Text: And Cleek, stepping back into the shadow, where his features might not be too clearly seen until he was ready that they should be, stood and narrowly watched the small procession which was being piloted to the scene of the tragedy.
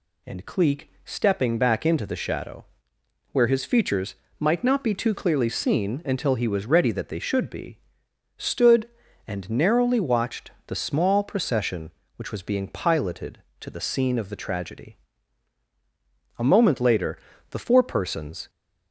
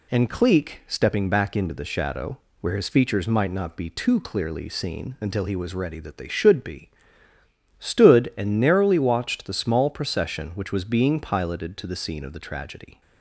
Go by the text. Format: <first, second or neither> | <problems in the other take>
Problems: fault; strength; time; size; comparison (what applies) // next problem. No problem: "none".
second | pauses between "features" and "might"; slight; at 4.1 s; 0.22 s long // pauses between "watched" and "the"; slight; at 10.5 s; 0.16 s long // goes on to say "A moment later the four persons"; strong; from 16.3 s on; 2.1 s long